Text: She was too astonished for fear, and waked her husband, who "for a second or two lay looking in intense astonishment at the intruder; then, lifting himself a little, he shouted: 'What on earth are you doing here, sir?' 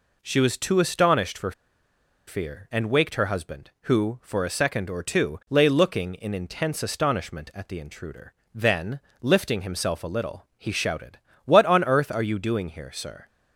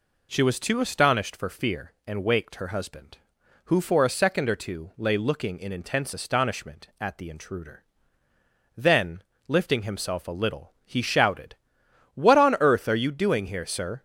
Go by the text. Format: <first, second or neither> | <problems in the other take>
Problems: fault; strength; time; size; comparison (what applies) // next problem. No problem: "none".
second | pauses between "for" and "fear"; noticeable; at 1.5 s; 0.76 s long